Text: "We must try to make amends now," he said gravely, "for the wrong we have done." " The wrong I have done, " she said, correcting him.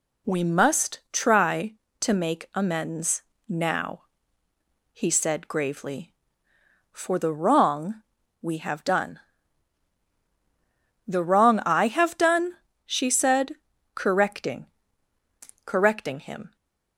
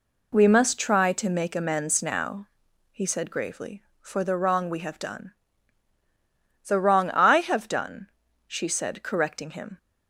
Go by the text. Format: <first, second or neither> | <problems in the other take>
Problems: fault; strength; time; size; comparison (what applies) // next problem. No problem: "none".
second | pauses between "amends" and "now"; slight; at 3.2 s; 0.26 s long // pauses between "wrong" and "we"; at 8.0 s; 0.40 s long // says "correcting" twice; at 15.6 s